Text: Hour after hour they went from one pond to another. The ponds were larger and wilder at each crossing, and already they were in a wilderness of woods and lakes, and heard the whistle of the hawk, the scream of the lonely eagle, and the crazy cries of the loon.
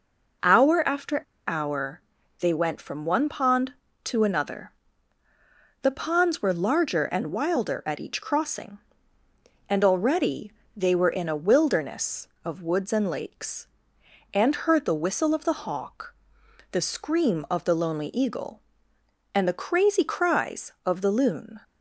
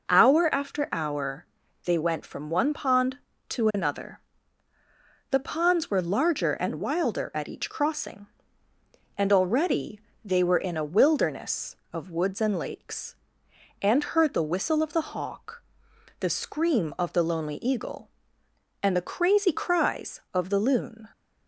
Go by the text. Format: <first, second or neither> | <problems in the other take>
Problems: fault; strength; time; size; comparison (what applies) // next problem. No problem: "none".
second | pauses between "after" and "hour"; slight; at 1.2 s; 0.25 s long // pauses between "hour" and "they"; at 2.0 s; 0.38 s long; also in the second // pauses between "already" and "they"; slight; at 10.5 s; 0.26 s long; slight in the second